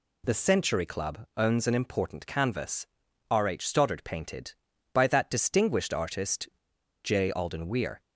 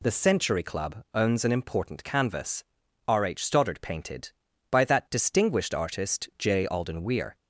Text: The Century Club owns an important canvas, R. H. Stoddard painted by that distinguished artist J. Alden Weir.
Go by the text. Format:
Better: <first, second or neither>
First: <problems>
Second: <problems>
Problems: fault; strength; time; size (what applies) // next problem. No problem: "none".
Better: second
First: pauses between "artist" and "J"; noticeable; at 6.4 s; 0.55 s long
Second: none